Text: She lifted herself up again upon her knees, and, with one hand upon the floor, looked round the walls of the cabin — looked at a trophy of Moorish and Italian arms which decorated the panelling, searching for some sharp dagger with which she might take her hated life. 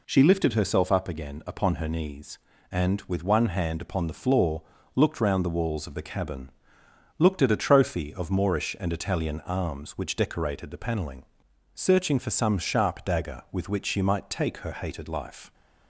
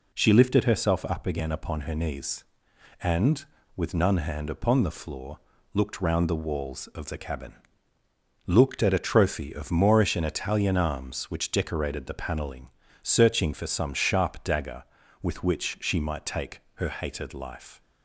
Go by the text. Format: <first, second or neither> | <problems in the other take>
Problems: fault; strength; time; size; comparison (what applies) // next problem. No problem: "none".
first | says "none" for "one"; at 3.9 s